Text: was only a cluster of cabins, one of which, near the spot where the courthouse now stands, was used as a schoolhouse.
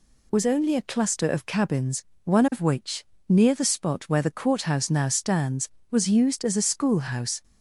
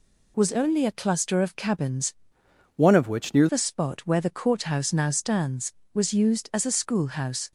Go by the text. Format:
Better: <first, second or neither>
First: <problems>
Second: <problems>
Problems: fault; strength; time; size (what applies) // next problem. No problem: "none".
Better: first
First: none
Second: changes voice from "one" to "near"; from 2.7 to 3.4 s; 0.7 s long